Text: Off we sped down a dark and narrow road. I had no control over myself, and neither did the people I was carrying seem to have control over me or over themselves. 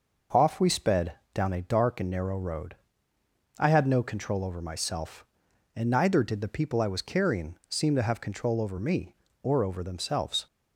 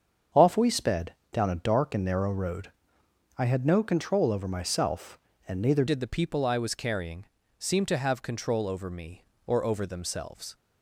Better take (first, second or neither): first